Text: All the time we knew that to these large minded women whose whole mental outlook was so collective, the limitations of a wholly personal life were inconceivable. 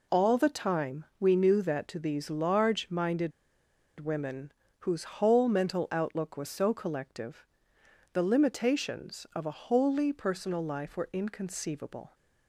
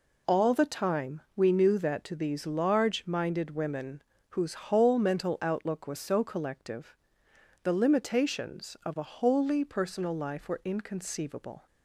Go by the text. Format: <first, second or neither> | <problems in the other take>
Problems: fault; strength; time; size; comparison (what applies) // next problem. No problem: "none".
second | pauses between "time" and "we"; slight; at 1.0 s; 0.16 s long; slight in the second // pauses between "minded" and "women"; noticeable; at 3.3 s; 0.69 s long // pauses between "women" and "whose"; slight; at 4.5 s; 0.30 s long; slight in the second